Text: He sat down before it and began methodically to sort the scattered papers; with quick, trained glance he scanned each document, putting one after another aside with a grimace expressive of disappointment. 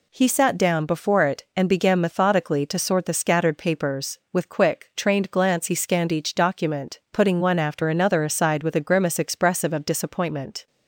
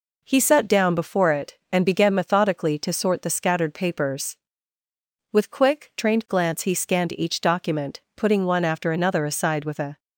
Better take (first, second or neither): first